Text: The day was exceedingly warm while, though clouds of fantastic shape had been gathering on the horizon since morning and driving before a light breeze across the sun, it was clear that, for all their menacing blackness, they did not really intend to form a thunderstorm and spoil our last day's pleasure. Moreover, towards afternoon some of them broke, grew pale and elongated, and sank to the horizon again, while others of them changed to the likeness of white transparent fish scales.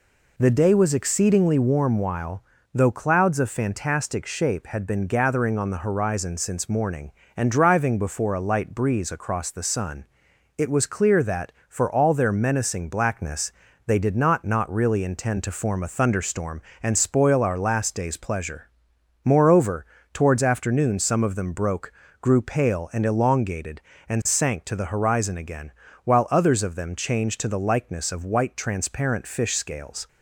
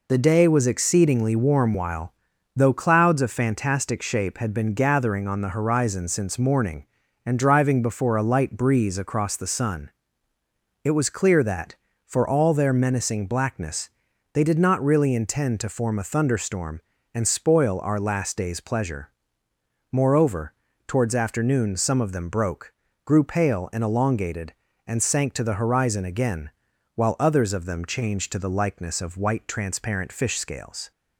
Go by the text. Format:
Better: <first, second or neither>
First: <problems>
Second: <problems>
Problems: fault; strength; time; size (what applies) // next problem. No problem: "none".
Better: second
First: says "not" twice; at 14.4 s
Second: none